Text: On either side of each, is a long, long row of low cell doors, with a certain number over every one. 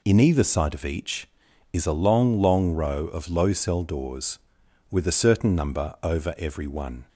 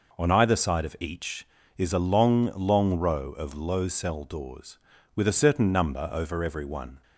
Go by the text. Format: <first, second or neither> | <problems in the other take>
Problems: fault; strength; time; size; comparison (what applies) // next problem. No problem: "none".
second | says "In" for "On"; at 0.0 s